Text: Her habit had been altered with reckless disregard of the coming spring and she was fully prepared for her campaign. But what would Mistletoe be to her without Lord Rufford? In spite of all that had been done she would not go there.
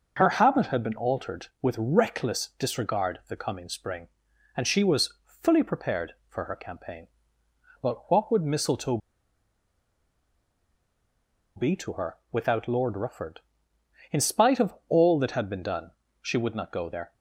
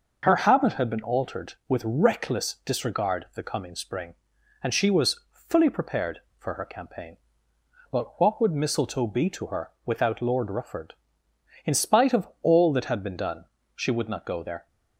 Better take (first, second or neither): second